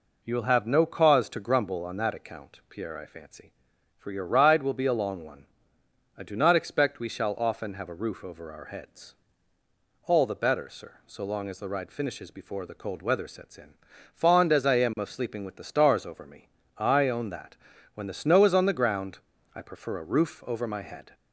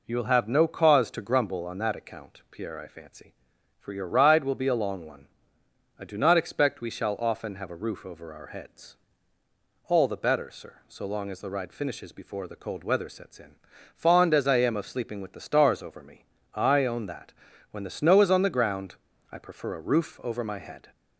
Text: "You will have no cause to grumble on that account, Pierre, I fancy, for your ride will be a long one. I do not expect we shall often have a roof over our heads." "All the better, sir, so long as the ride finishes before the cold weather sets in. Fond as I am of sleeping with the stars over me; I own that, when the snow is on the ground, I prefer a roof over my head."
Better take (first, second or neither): neither